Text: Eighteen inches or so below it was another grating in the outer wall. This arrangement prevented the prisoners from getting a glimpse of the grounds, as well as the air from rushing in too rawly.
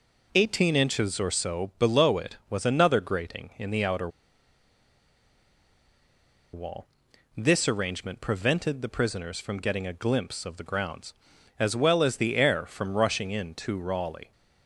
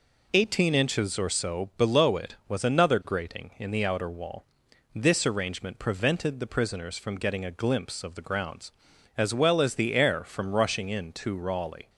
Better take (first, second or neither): second